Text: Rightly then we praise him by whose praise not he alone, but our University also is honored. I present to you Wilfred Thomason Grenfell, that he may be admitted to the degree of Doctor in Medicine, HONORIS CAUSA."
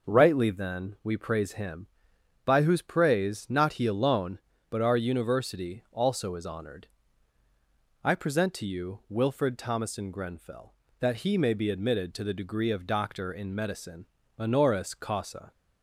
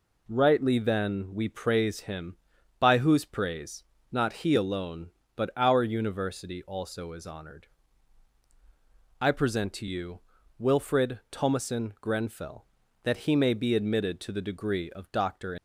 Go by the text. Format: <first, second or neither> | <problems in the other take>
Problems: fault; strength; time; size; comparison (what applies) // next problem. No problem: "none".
first | pauses between "praise" and "not"; slight; at 3.8 s; 0.28 s long // pauses between "you" and "Wilfred"; at 10.1 s; 0.40 s long // stops before "in Medicine HONORIS CAUSA"; at 15.5 s